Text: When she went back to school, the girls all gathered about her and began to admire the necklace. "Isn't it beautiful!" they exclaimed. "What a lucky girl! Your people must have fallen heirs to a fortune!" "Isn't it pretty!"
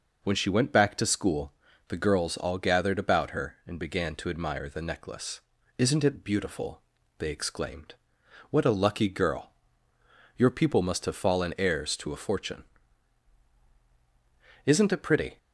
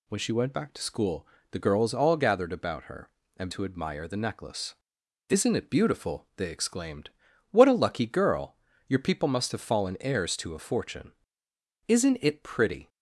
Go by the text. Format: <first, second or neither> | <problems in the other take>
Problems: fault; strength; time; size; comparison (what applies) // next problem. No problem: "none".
first | skips "began"; at 3.5 s